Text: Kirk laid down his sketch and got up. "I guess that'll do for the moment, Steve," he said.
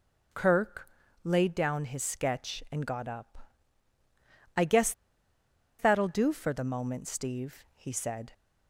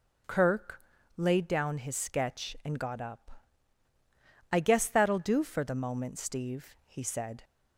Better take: second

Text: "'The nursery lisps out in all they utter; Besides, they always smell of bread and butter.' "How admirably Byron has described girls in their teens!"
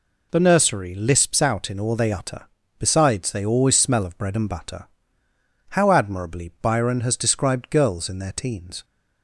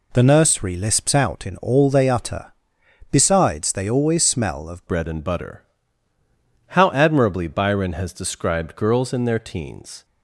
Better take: first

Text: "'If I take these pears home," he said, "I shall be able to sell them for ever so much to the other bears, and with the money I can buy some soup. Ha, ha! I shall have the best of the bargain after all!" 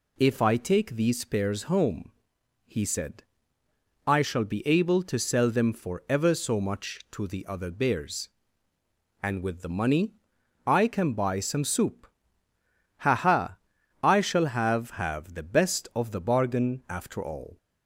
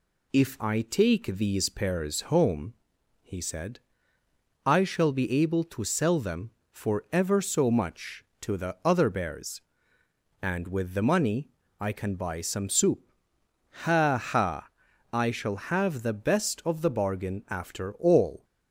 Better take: second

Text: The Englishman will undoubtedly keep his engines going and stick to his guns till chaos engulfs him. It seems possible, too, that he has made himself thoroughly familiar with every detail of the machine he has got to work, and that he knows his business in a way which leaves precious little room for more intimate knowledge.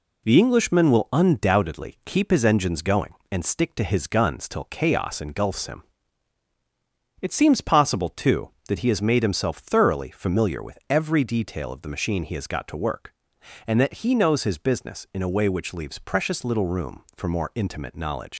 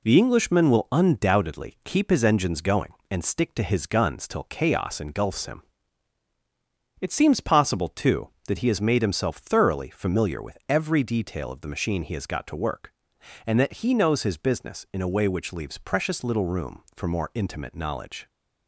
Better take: second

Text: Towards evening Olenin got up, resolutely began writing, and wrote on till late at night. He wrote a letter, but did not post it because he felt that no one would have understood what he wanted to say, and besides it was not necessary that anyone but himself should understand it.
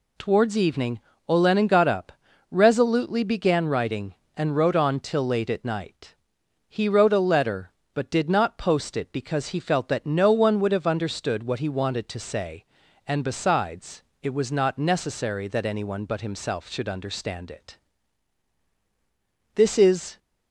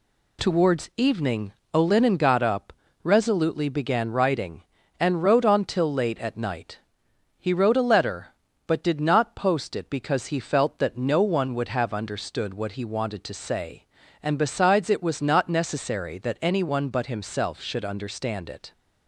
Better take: second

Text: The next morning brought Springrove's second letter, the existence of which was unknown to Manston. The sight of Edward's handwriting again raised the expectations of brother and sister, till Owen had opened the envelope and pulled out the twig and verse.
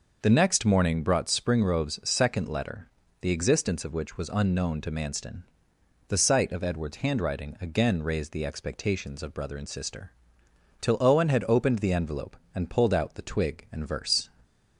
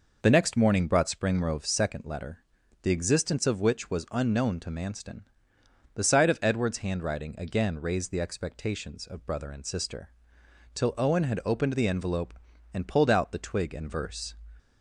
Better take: neither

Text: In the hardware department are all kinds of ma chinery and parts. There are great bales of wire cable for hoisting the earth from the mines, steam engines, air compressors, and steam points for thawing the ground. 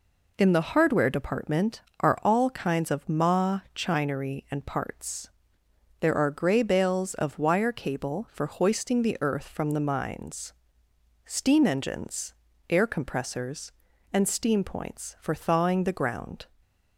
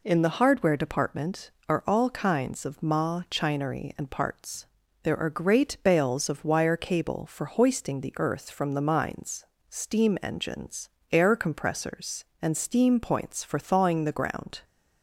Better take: second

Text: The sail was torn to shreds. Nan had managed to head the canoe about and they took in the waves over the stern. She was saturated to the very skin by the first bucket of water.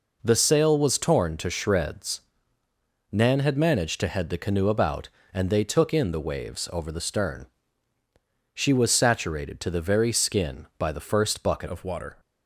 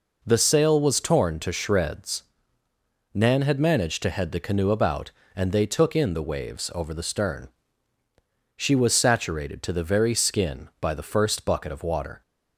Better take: second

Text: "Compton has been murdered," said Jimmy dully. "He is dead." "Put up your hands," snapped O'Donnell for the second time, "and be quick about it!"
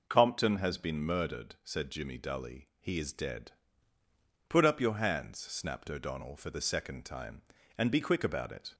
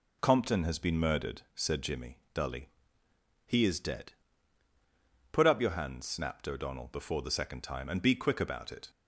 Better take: first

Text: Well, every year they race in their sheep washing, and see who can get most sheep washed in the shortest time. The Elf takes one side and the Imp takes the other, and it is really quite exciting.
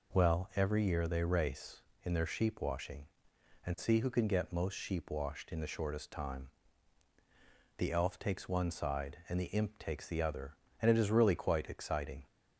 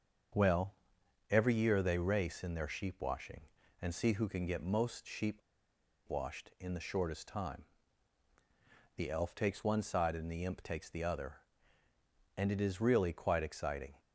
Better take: first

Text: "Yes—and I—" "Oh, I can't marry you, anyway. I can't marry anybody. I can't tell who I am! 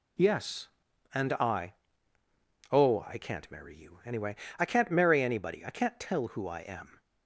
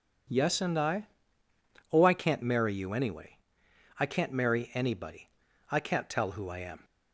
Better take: neither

